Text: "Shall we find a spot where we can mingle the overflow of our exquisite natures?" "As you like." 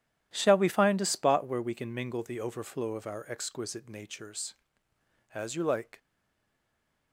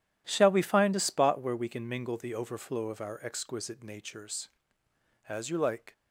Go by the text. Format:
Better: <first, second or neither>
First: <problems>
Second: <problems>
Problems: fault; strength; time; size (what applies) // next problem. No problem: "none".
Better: second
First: stays silent after the last word; from 5.9 s on; 1.2 s long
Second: none